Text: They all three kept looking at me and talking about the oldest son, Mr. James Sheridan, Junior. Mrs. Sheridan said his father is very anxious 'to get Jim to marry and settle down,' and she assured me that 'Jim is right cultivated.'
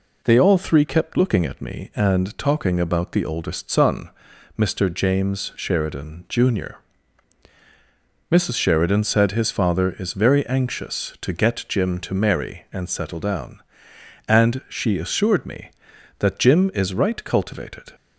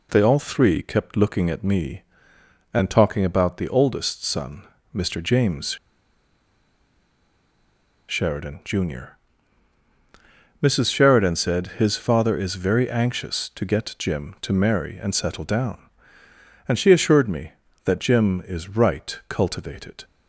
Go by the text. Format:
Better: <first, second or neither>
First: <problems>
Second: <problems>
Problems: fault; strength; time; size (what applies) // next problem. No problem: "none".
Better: first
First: none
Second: pauses between "James" and "Sheridan"; strong; at 5.7 s; 2.3 s long